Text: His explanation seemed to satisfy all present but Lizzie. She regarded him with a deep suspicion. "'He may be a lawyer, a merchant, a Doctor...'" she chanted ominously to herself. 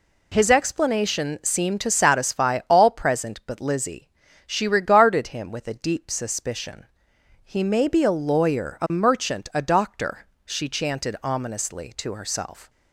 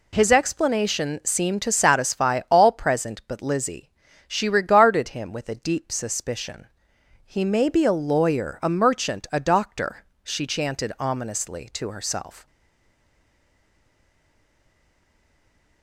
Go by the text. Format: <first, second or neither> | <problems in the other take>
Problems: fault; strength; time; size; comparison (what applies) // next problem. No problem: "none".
first | stays silent after the last word; strong; from 12.4 s on; 3.4 s long